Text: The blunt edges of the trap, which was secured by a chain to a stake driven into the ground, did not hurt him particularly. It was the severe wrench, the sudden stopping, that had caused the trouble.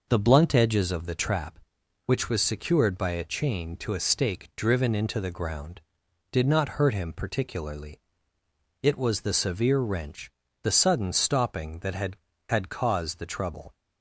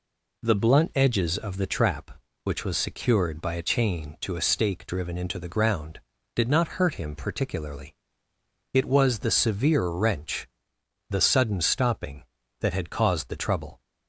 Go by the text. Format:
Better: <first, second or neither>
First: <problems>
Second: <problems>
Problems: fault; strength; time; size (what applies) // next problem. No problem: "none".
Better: second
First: says "had" twice; at 12.4 s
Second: none